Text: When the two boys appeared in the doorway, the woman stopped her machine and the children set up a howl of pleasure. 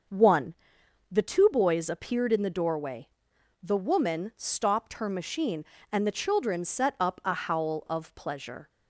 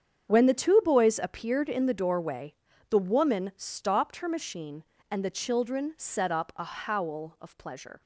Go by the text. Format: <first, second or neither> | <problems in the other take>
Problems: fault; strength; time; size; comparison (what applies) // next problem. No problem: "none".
second | starts louder than the rest; until 1.7 s; 6.5 dB; strong in the second // says "One" for "When"; at 0.0 s